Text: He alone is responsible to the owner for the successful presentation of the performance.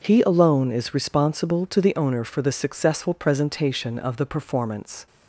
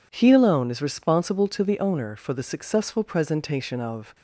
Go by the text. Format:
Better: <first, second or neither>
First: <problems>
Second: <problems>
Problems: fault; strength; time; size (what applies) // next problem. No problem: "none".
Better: first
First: none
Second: stops before "the performance"; at 4.1 s